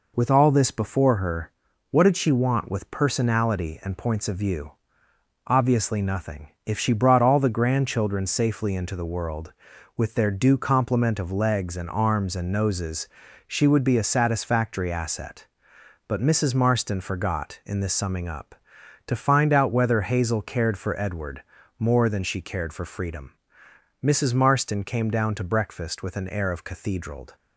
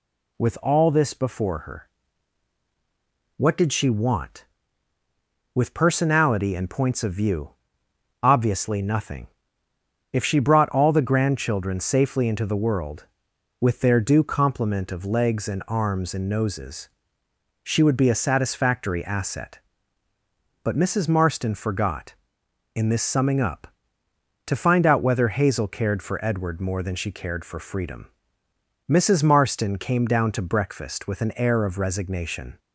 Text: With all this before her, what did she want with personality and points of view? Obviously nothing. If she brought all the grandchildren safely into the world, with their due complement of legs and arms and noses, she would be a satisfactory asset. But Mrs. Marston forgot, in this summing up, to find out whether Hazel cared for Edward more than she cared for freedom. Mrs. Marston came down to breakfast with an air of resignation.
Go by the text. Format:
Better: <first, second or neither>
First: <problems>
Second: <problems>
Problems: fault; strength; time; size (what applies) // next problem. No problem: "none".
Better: second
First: pauses between "Edward" and "more"; slight; at 21.4 s; 0.34 s long // says "cathedraled" for "resignation"; at 26.6 s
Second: none